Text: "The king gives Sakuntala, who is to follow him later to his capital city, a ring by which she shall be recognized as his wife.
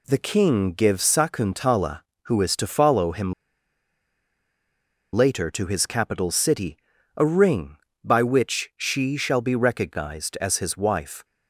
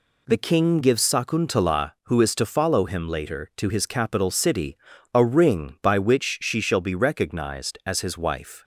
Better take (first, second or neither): second